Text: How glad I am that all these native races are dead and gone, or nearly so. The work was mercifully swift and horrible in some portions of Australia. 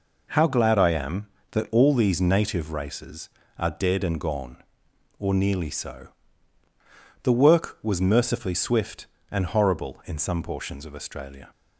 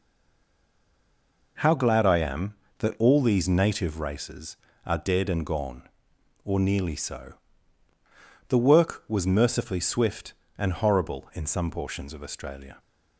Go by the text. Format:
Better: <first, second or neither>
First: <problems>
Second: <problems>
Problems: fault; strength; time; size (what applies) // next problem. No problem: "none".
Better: first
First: none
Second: stays silent before the first word; noticeable; until 1.5 s; 1.5 s long